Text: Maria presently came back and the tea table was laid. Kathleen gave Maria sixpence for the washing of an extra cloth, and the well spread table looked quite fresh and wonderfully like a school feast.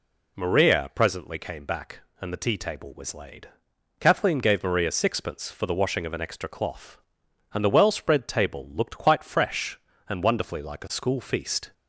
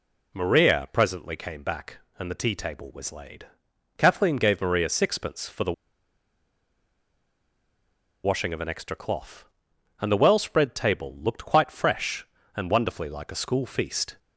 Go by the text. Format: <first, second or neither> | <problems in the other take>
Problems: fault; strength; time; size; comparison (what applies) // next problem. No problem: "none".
first | pauses between "the" and "washing"; strong; at 5.7 s; 2.5 s long